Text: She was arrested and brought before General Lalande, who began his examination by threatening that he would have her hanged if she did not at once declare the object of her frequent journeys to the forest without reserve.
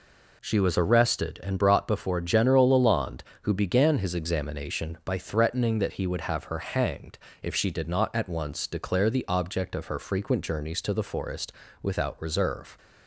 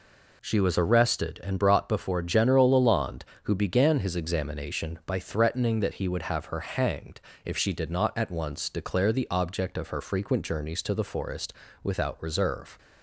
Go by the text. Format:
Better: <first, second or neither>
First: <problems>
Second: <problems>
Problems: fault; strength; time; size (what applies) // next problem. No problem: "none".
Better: neither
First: pauses between "hanged" and "if"; slight; at 7.1 s; 0.26 s long // pauses between "forest" and "without"; slight; at 11.5 s; 0.28 s long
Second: pauses between "hanged" and "if"; slight; at 7.1 s; 0.26 s long // pauses between "forest" and "without"; slight; at 11.5 s; 0.28 s long